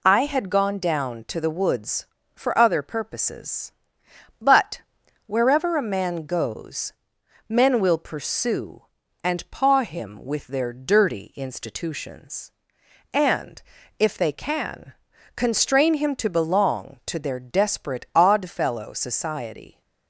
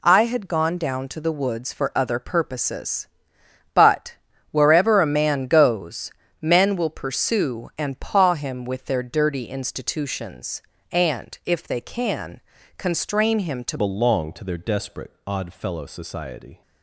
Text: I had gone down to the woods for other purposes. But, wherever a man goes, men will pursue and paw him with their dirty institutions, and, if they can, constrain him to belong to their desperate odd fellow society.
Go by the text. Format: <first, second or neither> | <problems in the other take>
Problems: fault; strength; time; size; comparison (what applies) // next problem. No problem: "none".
first | changes voice at "belong"; from 13.7 s on; 2.9 s long // pauses between "desperate" and "odd"; slight; at 15.1 s; 0.16 s long